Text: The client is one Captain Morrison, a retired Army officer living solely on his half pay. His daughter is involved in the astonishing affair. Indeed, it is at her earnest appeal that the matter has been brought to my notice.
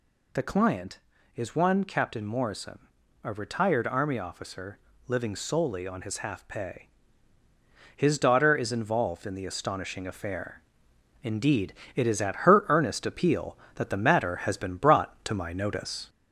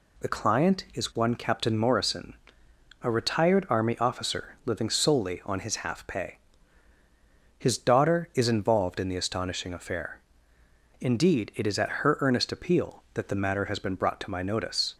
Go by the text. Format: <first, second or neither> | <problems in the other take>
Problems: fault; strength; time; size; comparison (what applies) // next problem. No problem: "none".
second | gets louder; slight; throughout; 2 dB // pauses between "officer" and "living"; slight; at 4.7 s; 0.30 s long